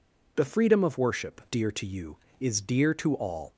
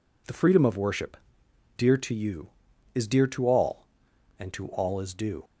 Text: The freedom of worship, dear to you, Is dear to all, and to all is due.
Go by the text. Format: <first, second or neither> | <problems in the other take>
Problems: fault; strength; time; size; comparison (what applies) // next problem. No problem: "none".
second | stops before "and to all is due"; at 3.5 s